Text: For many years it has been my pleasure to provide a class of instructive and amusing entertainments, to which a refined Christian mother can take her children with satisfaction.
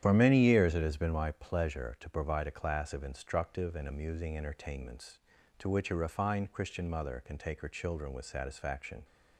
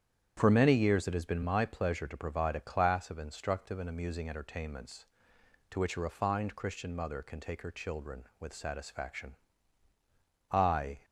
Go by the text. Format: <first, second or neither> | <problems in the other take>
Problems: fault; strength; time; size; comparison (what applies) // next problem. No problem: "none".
first | starts louder than the rest; strong; until 1.3 s; 9 dB; strong in the first // goes on to say "I"; from 10.5 s on; 0.54 s long